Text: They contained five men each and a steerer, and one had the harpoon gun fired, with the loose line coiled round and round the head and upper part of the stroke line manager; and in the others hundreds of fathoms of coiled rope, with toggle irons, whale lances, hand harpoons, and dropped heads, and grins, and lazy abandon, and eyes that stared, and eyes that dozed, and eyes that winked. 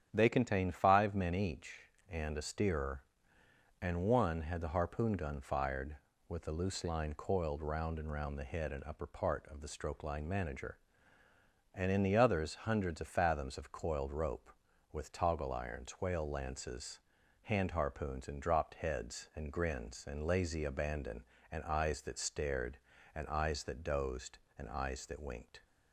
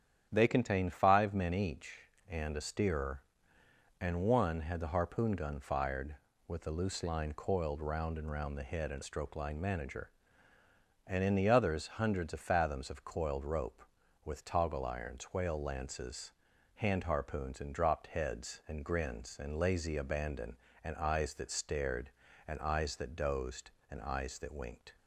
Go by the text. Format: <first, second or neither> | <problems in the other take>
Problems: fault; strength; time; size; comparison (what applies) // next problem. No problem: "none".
first | starts louder than the rest; strong; until 1.3 s; 9.5 dB; strong in the first // skips "upper part of the"; at 9.0 s